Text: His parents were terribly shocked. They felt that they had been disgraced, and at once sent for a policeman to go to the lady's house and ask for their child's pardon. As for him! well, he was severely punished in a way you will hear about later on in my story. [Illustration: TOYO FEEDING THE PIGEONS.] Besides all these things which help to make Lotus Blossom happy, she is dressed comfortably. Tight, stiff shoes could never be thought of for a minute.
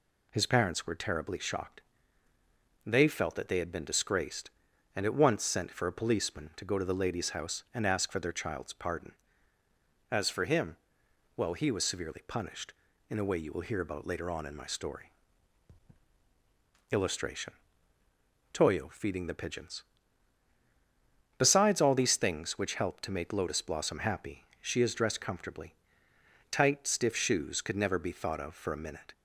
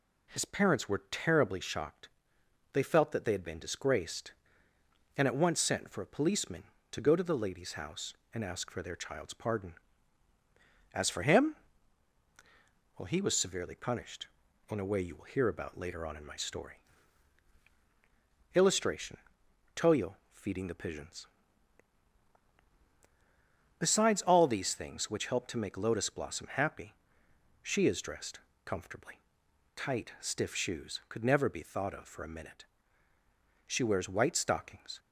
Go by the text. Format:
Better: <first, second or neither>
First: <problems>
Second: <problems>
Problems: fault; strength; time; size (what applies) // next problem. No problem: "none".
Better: first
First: none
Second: pauses between "TOYO" and "FEEDING"; slight; at 20.1 s; 0.18 s long // pauses between "dressed" and "comfortably"; slight; at 28.4 s; 0.24 s long // goes on to say "She wears white stockings"; from 33.6 s on; 1.3 s long